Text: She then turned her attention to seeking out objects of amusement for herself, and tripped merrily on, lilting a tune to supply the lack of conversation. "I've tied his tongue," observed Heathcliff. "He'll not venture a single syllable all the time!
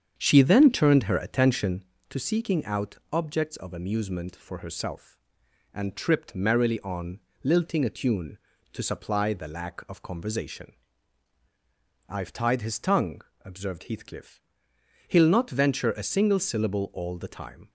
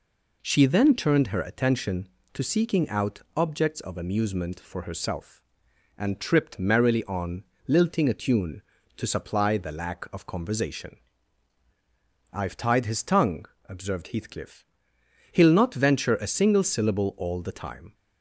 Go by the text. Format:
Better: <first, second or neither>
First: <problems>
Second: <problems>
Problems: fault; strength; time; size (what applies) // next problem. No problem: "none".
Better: second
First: starts louder than the rest; strong; until 1.8 s; 8 dB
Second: none